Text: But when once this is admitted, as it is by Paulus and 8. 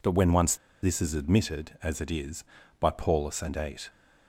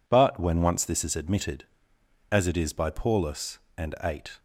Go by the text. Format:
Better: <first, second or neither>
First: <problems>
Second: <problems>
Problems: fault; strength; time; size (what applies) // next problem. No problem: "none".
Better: second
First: pauses between "once" and "this"; slight; at 0.5 s; 0.27 s long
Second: none